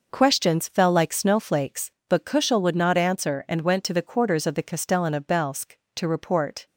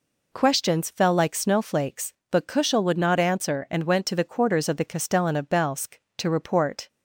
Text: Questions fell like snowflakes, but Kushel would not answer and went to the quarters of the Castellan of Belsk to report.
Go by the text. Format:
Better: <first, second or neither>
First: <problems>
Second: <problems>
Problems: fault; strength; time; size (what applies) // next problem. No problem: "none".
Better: second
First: gets quieter; strong; throughout; 10 dB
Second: none